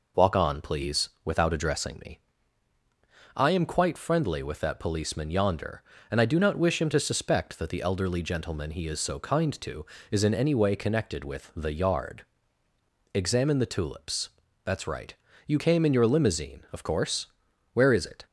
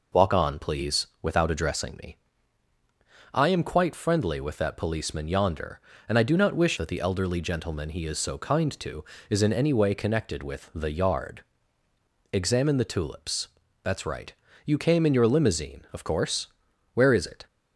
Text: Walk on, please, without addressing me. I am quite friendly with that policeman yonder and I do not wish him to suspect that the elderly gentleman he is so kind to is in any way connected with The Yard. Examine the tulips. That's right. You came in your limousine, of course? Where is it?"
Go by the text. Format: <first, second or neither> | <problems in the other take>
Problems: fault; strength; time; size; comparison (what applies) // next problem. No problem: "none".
first | skips "him to suspect"; at 6.7 s